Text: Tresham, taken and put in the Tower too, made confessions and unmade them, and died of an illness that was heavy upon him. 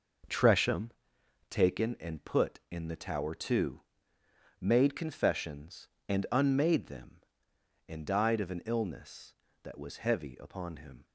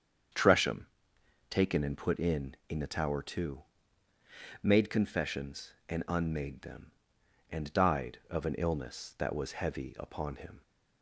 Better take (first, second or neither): first